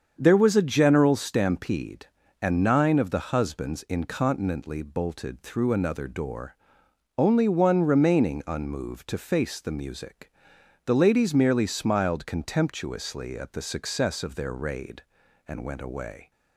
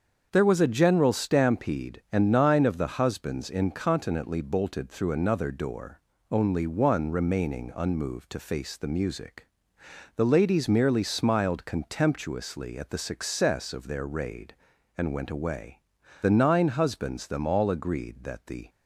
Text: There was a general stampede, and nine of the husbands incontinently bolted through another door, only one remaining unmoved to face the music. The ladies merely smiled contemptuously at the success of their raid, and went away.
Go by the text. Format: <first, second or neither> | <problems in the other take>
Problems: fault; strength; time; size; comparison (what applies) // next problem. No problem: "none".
first | starts louder than the rest; until 1.3 s; 7 dB; strong in the first // goes on to say "The nine husbands them all agreed that the"; strong; from 16.2 s on; 2.4 s long